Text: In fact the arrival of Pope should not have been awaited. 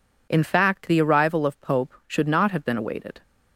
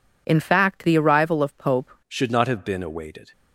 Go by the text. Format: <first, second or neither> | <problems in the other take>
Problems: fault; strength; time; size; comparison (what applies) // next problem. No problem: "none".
first | changes voice at "should"; from 2.0 s on; 1.3 s long